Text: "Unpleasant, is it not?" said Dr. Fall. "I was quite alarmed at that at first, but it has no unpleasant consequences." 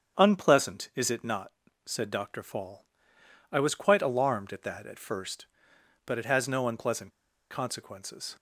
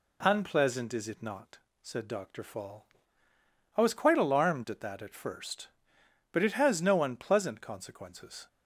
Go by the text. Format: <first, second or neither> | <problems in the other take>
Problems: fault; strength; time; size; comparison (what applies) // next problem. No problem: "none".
second | starts louder than the rest; strong; until 1.2 s; 7.5 dB // pauses between "unpleasant" and "consequences"; at 7.1 s; 0.39 s long